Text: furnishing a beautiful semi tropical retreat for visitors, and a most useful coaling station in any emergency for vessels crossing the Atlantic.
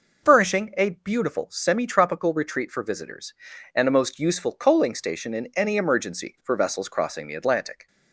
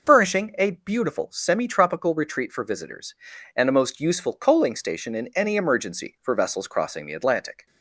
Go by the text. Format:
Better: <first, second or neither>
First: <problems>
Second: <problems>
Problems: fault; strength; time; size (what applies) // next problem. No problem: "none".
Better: neither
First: none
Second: none